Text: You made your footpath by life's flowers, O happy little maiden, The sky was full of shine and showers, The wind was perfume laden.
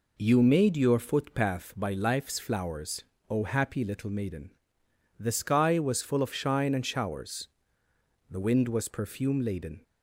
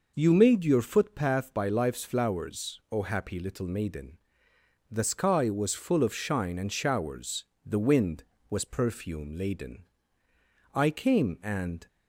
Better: first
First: none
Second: goes on to say "I came and"; noticeable; from 10.7 s on; 1.1 s long

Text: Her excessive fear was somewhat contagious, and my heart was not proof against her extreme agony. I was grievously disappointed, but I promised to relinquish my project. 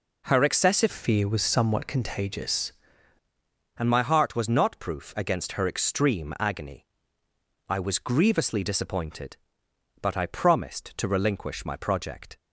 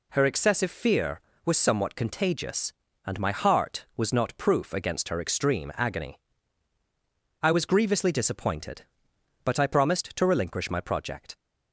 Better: second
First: changes voice from "fear" to "contagious"; from 0.9 to 2.7 s; 1.8 s long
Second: none

